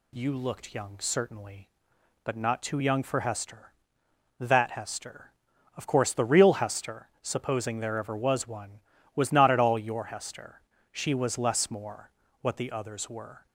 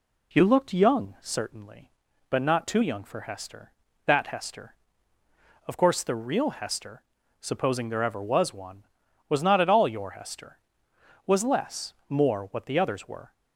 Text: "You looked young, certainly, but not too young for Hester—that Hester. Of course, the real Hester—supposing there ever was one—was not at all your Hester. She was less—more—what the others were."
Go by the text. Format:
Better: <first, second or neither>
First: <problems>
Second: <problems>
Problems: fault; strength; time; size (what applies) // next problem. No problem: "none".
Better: first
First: none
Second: skips "She"; at 10.9 s